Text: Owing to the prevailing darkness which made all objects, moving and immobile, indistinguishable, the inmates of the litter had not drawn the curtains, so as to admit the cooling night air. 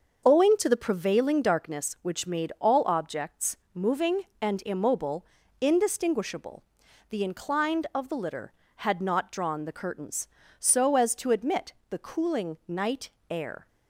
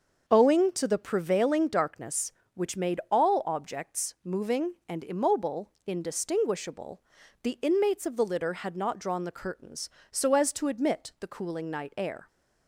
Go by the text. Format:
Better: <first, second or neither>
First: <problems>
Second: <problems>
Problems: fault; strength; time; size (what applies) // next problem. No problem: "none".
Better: second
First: starts louder than the rest; until 1.2 s; 6.5 dB // says "inclined" for "inmates"; at 7.2 s // pauses between "admit" and "the"; slight; at 11.7 s; 0.16 s long // pauses between "night" and "air"; slight; at 13.0 s; 0.20 s long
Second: starts louder than the rest; until 1.2 s; 6.5 dB